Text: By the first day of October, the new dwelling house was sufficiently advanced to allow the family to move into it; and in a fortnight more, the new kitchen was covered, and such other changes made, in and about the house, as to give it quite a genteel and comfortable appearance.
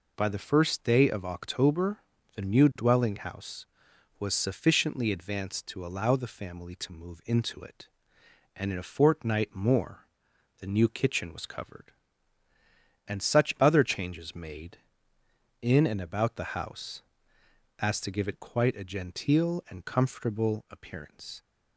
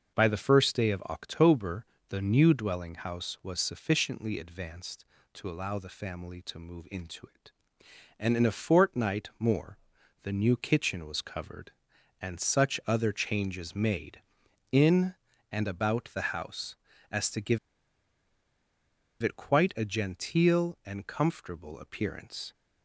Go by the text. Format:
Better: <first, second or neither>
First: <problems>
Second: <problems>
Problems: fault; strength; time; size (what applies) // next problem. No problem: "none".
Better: first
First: none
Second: pauses between "give" and "it"; strong; at 17.5 s; 1.6 s long